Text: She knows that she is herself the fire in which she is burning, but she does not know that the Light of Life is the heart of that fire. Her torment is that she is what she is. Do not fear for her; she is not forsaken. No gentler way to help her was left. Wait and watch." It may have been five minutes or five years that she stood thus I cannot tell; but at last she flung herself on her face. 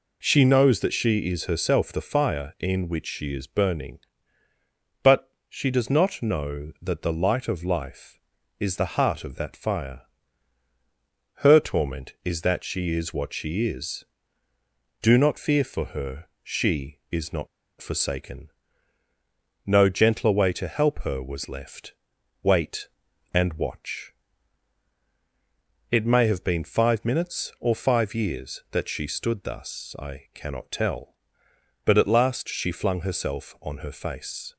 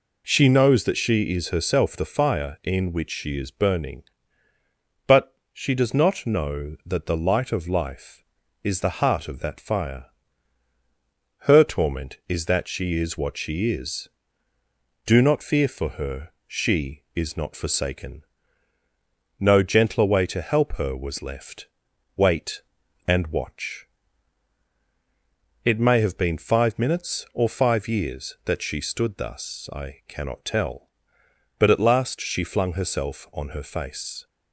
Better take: second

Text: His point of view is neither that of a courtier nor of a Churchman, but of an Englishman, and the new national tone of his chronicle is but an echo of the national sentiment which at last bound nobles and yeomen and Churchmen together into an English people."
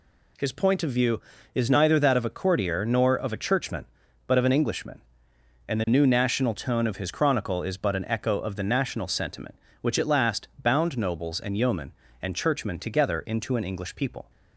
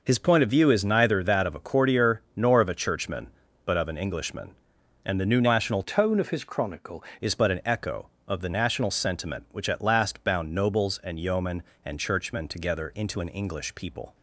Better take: first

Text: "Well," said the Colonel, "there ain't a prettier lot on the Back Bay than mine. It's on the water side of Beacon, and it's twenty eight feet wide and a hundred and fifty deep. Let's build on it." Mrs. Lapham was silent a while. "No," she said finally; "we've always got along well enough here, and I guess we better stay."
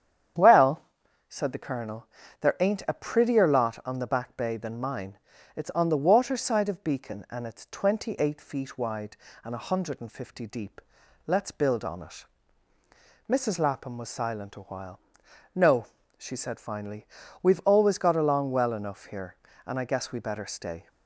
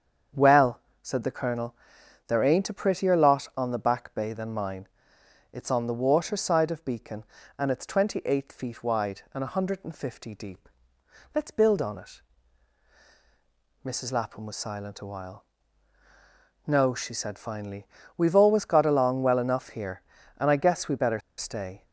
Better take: first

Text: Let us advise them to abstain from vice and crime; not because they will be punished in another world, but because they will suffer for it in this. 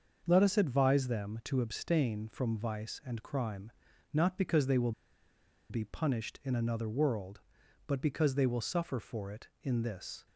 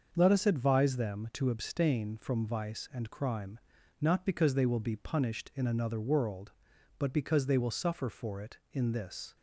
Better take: second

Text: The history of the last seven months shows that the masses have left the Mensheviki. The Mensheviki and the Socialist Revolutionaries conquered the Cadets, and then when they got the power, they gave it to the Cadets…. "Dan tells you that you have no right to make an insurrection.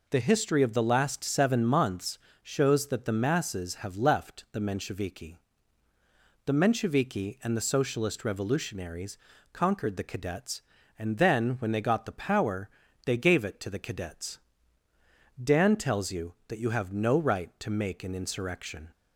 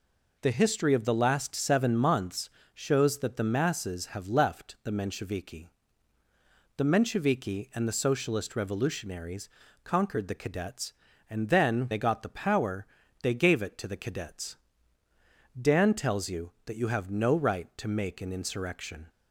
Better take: first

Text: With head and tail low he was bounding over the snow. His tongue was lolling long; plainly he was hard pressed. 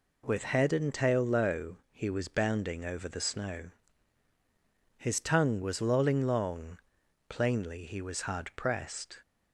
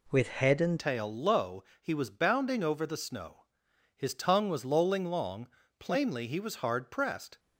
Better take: first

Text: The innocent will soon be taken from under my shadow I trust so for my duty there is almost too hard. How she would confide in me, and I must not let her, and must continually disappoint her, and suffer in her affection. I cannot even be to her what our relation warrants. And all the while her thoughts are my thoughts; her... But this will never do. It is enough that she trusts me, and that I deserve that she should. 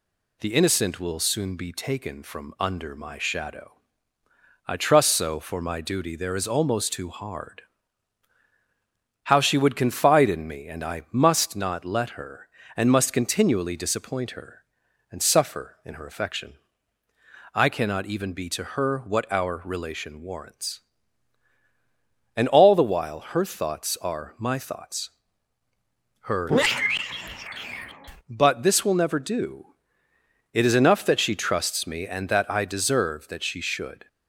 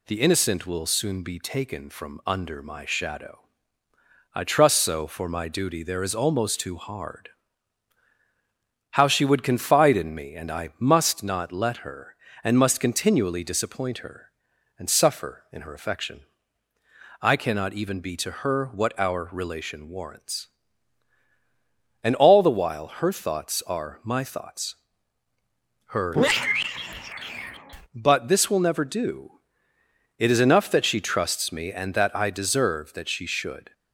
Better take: neither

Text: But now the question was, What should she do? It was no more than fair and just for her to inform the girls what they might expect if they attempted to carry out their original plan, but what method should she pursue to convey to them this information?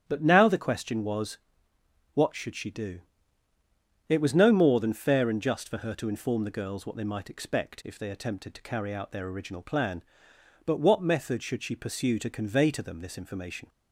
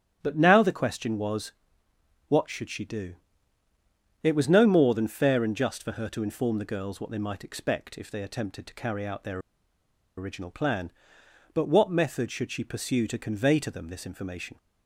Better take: first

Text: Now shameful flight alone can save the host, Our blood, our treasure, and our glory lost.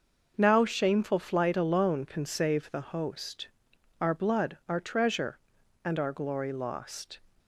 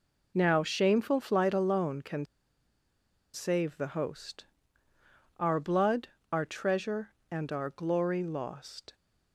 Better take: first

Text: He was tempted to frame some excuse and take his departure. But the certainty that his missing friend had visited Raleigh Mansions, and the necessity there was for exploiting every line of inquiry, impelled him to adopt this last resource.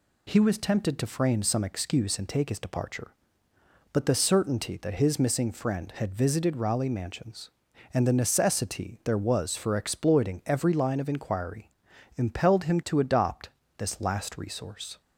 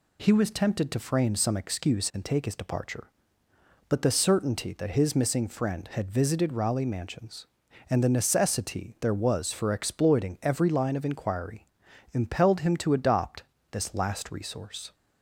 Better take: neither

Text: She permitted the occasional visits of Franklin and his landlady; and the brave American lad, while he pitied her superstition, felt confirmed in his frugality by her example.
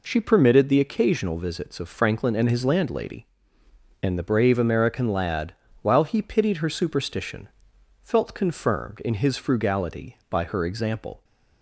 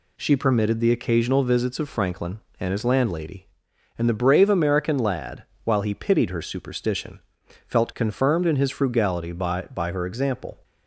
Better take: first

